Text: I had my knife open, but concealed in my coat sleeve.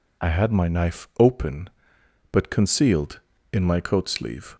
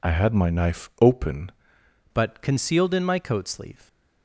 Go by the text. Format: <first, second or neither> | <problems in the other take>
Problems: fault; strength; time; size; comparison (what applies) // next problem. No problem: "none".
first | changes voice at "but"; from 2.1 s on; 1.7 s long